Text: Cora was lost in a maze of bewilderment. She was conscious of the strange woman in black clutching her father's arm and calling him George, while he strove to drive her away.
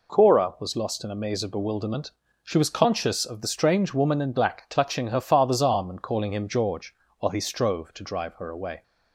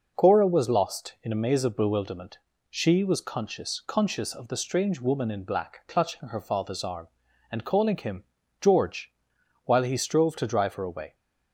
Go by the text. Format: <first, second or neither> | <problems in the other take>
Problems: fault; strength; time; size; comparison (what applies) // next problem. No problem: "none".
first | says "conscious" twice; at 3.8 s // pauses between "him" and "George"; at 8.2 s; 0.38 s long